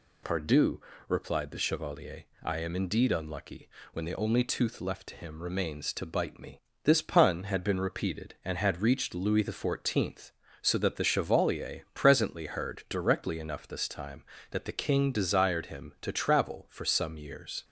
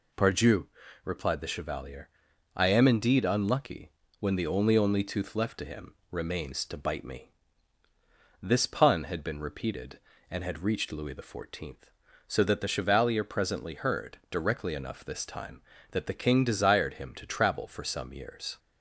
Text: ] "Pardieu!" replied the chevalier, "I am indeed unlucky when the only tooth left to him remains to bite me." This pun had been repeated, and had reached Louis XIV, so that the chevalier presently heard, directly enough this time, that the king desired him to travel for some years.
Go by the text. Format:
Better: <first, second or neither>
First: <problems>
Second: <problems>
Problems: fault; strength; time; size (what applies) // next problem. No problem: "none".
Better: first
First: pauses between "unlucky" and "when"; slight; at 3.6 s; 0.24 s long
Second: pauses between "unlucky" and "when"; slight; at 3.9 s; 0.26 s long // says "only" twice; at 4.7 s // pauses between "him" and "remains"; slight; at 5.9 s; 0.16 s long